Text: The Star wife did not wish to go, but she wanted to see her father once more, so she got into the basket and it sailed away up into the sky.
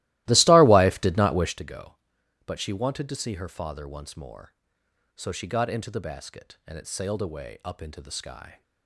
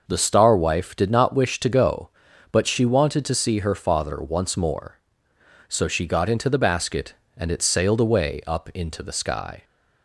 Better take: second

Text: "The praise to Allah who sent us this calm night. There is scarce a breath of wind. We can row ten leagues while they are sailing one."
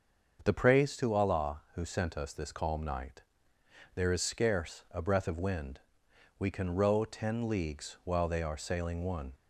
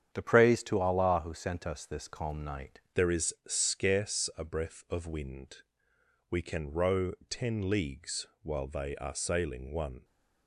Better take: first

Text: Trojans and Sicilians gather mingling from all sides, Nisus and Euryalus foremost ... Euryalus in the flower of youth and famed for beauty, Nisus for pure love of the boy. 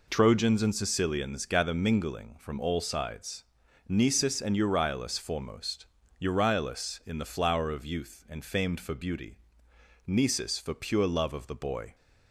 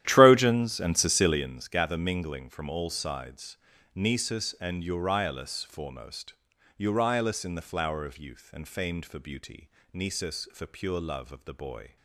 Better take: first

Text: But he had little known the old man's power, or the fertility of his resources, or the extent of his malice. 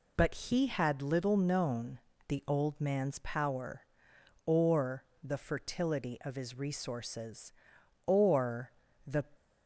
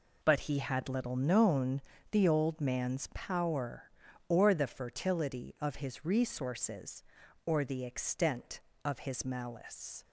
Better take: second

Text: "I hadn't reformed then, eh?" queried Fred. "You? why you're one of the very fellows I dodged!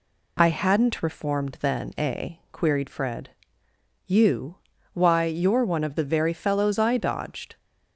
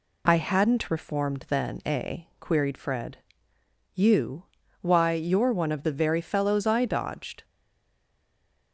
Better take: first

